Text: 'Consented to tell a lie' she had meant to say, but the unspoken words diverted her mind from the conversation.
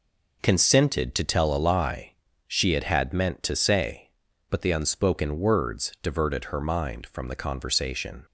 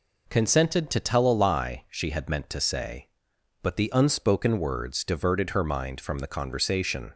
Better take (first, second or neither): second